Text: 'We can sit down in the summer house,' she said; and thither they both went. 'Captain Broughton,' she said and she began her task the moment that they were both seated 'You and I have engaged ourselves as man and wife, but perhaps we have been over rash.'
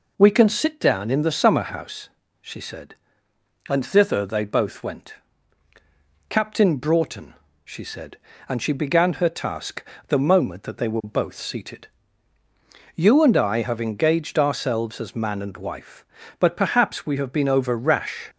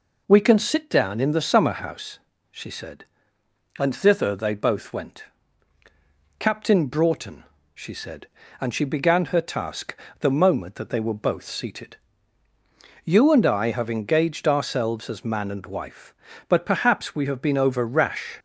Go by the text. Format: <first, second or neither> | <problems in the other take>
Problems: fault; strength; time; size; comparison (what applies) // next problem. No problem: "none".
neither | pauses between "task" and "the"; slight; the same in both // pauses between "seated" and "You"; the same in both